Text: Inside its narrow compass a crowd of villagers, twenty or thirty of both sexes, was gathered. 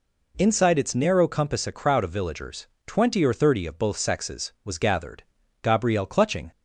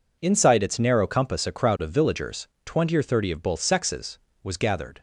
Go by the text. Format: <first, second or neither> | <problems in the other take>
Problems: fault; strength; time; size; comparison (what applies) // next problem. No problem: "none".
second | goes on to say "Gabrielle clutching"; noticeable; from 5.6 s on; 0.88 s long